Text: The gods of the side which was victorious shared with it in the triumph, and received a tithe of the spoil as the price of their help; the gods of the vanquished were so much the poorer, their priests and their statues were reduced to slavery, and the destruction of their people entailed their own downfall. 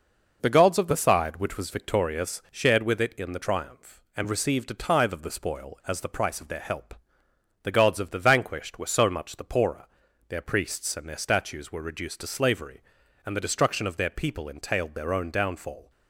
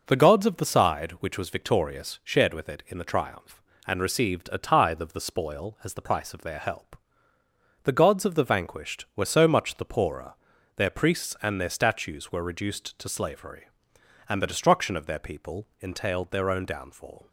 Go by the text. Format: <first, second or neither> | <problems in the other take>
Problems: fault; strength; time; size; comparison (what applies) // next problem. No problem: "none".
neither | none